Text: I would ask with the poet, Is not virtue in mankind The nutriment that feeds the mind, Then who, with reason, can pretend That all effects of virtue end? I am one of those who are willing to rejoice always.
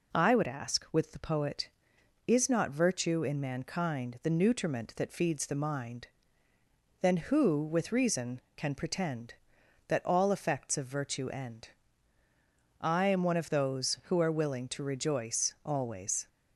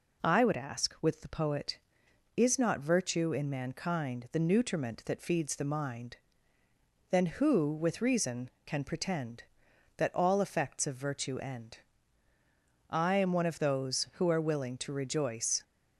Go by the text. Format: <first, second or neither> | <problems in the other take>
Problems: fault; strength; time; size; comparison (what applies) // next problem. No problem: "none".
first | stops before "always"; at 15.6 s